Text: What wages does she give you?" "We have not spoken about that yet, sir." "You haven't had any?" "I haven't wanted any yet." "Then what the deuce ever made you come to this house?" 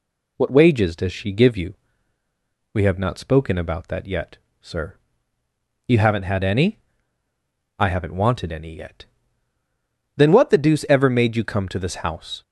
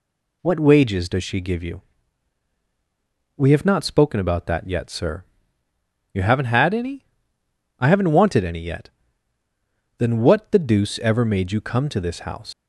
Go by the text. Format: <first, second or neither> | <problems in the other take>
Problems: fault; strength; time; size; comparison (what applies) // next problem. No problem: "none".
first | leaves "house" unfinished; at 12.5 s; 115 ms